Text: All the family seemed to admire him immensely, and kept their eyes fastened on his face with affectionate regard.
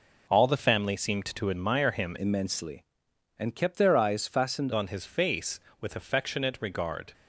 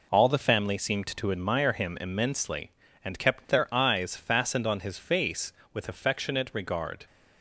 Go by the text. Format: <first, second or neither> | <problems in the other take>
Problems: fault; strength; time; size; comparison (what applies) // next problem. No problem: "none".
second | changes voice from "immensely" to "fastened"; from 2.1 to 4.6 s; 2.5 s long